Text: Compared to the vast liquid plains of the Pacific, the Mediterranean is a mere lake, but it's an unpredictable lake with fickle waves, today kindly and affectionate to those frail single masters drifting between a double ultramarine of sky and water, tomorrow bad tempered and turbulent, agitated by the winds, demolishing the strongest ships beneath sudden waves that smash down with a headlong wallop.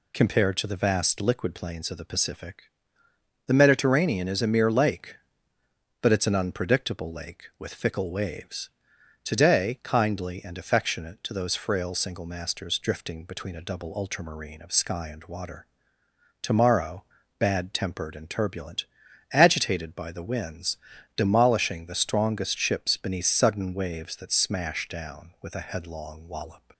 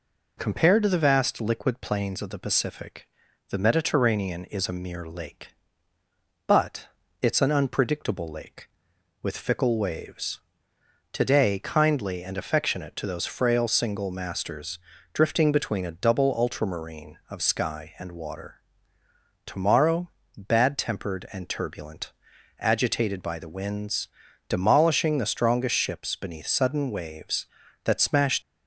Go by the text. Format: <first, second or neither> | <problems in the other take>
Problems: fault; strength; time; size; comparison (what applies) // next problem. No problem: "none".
first | pauses between "but" and "it's"; slight; at 6.8 s; 0.34 s long // pauses between "masters" and "drifting"; slight; at 14.7 s; 0.34 s long // pauses between "tomorrow" and "bad"; slight; at 20.0 s; 0.28 s long; slight in the first // stops before "down with a headlong wallop"; at 28.4 s